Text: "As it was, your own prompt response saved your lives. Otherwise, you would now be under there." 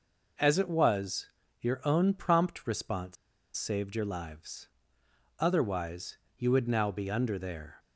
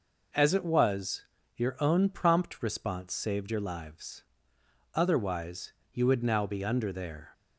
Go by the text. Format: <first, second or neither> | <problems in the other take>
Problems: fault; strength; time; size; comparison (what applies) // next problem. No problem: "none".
second | pauses between "response" and "saved"; at 3.1 s; 0.41 s long